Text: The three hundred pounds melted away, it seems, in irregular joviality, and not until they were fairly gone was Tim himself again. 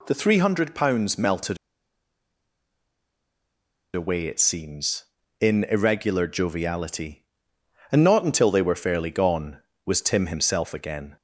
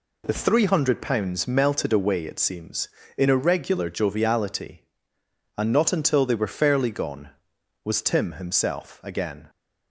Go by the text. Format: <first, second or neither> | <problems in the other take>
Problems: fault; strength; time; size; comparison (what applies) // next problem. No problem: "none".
second | pauses between "melted" and "away"; strong; at 1.5 s; 2.3 s long